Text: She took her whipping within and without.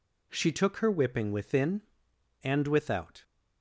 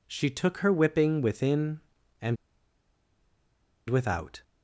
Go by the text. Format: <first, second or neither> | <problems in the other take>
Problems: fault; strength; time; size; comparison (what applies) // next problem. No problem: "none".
first | pauses between "and" and "without"; strong; at 2.3 s; 1.5 s long